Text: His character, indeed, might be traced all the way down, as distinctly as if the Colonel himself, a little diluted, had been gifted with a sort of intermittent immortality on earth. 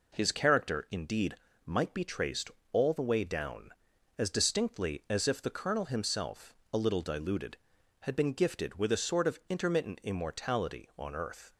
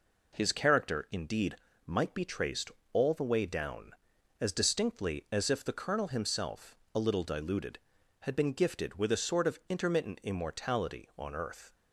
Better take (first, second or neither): neither